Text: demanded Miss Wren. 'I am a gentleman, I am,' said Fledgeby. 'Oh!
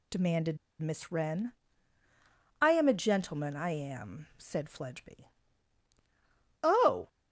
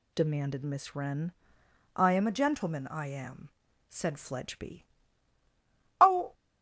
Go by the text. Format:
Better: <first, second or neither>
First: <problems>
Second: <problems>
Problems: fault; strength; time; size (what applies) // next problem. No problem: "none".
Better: second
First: pauses between "demanded" and "Miss"; slight; at 0.5 s; 0.24 s long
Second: none